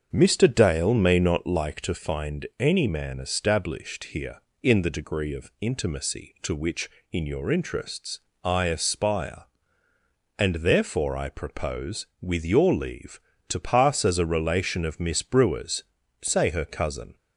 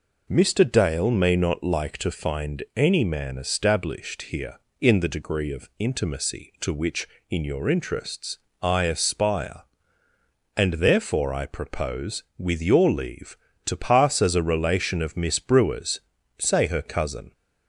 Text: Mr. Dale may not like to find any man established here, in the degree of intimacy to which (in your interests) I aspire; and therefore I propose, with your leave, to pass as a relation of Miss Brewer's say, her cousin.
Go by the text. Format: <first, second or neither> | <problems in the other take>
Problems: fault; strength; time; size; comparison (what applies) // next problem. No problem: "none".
second | starts louder than the rest; until 1.6 s; 7 dB // pauses between "Brewer's" and "say"; at 15.8 s; 0.38 s long; also in the second